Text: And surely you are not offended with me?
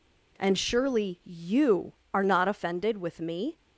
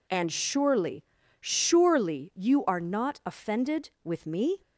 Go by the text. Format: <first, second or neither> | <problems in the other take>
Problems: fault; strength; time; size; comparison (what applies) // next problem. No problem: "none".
first | says "surely" twice; at 1.4 s